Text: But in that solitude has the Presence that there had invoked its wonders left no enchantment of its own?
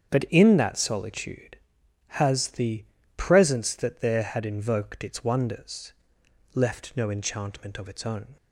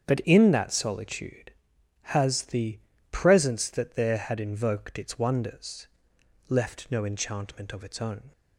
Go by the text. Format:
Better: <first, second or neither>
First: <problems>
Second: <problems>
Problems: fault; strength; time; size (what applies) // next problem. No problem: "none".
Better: neither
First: starts louder than the rest; strong; until 1.1 s; 7.5 dB // pauses between "the" and "Presence"; slight; at 2.8 s; 0.32 s long // pauses between "wonders" and "left"; noticeable; at 5.9 s; 0.64 s long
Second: starts louder than the rest; strong; until 1.1 s; 7.5 dB // pauses between "the" and "Presence"; slight; at 2.7 s; 0.32 s long // pauses between "wonders" and "left"; noticeable; at 5.8 s; 0.64 s long